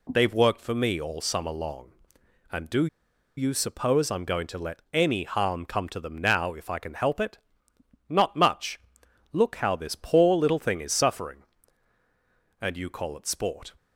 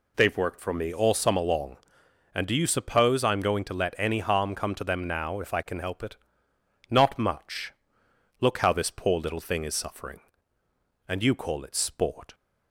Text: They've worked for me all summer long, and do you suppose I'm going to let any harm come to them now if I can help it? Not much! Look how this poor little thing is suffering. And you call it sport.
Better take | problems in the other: second | pauses between "do" and "you"; noticeable; at 2.8 s; 0.51 s long

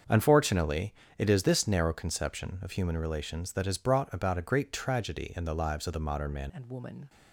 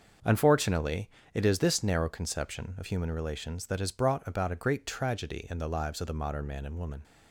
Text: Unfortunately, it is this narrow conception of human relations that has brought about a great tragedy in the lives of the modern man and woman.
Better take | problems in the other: second | starts louder than the rest; until 1.3 s; 7 dB; also in the second // changes voice at "and"; from 6.5 s on; 0.5 s long

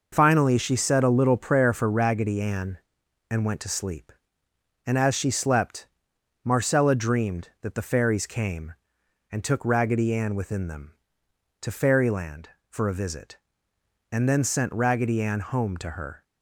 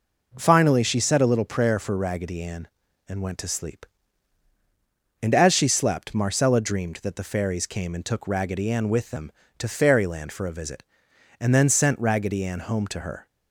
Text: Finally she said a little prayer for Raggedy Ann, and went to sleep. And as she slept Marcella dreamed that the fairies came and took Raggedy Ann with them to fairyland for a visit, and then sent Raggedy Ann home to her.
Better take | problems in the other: second | pauses between "slept" and "Marcella"; noticeable; at 5.8 s; 0.56 s long // says "within" for "with"; at 10.3 s

